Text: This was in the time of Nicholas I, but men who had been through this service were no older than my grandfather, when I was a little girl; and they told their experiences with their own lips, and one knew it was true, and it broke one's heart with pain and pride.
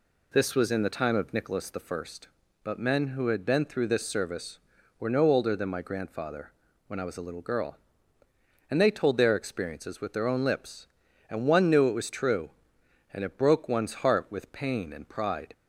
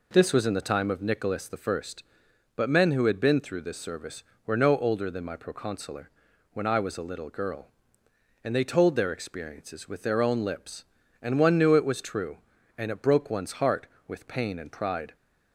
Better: first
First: none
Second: says "proconsular" for "grandfather"; at 5.3 s

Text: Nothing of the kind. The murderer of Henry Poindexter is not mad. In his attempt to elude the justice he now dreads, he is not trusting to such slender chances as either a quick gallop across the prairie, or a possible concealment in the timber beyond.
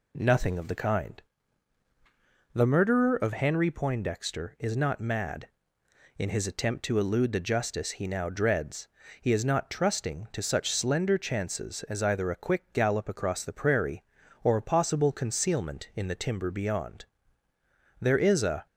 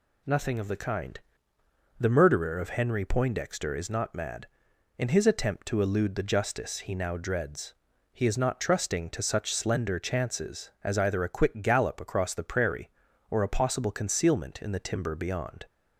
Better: second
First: goes on to say "There is a"; noticeable; from 17.9 s on; 0.66 s long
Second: none

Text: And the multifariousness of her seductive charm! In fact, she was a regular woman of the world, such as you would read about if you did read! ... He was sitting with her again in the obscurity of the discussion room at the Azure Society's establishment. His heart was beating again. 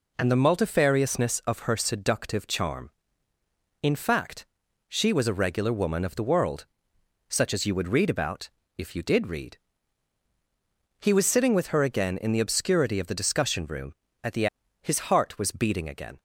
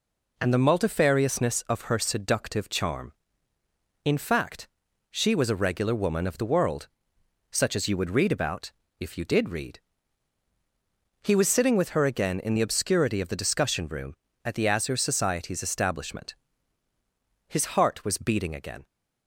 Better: second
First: pauses between "about" and "if"; slight; at 8.4 s; 0.30 s long // skips "Azure Society's establishment"; at 14.6 s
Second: pauses between "about" and "if"; slight; at 8.7 s; 0.30 s long

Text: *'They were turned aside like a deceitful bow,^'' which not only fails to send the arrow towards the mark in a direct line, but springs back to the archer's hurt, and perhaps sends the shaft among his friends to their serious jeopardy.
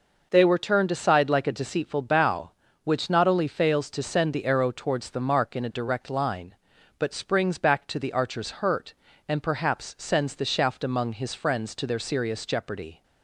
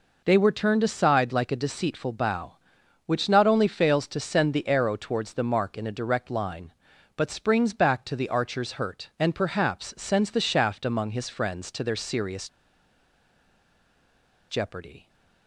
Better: first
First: none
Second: pauses between "serious" and "jeopardy"; strong; at 12.4 s; 2.0 s long

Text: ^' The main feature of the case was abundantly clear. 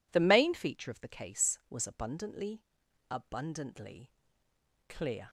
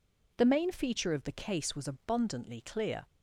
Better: second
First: says "abundantly" twice; at 3.0 s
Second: none

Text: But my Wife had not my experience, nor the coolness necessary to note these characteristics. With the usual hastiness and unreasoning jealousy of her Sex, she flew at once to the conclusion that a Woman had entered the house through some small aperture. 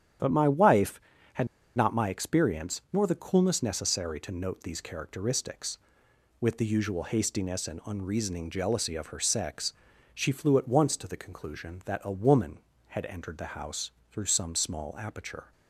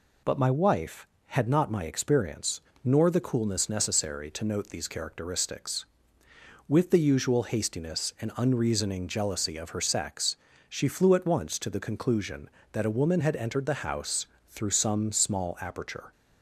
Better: second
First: starts louder than the rest; strong; until 1.8 s; 9.5 dB // pauses between "had" and "not"; slight; at 1.4 s; 0.29 s long // pauses between "house" and "through"; slight; at 13.9 s; 0.18 s long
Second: pauses between "house" and "through"; slight; at 14.2 s; 0.20 s long

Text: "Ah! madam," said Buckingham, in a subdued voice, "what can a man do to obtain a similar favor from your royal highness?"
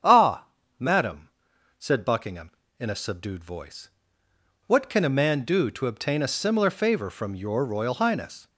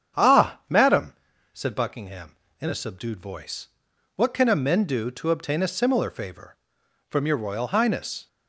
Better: first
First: starts louder than the rest; strong; until 1.8 s; 8 dB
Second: starts louder than the rest; strong; until 1.6 s; 8 dB // says "men" for "man"; at 4.5 s

